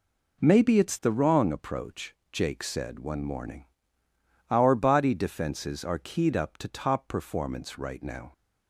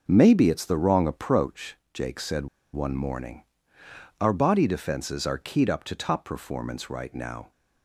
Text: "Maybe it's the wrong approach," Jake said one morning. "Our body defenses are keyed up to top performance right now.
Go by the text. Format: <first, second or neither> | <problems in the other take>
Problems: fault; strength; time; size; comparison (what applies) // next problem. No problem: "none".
first | starts louder than the rest; noticeable; until 1.0 s; 6 dB // pauses between "said" and "one"; slight; at 2.4 s; 0.27 s long